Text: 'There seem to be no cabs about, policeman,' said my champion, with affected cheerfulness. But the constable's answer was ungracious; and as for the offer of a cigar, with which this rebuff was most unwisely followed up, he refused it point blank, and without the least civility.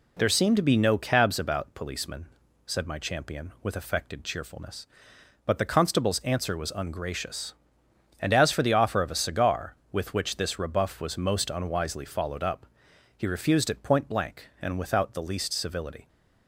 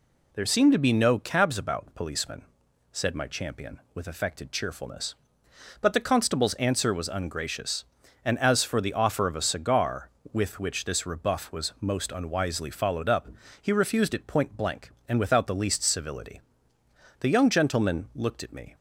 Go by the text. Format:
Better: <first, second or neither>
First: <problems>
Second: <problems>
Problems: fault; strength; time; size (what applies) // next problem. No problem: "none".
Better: first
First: none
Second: goes on to say "The young gentleman looked at me"; from 17.2 s on; 1.5 s long